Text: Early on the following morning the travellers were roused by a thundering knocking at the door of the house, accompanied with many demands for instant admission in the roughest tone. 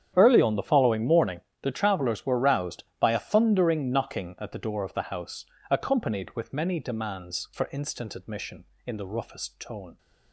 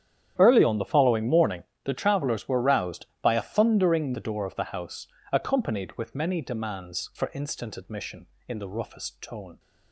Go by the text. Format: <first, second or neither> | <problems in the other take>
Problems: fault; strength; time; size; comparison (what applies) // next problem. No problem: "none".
first | starts louder than the rest; strong; until 1.4 s; 10 dB; strong in the first // pauses between "morning" and "the"; slight; at 1.6 s; 0.22 s long; slight in the first // skips "knocking at"; at 4.1 s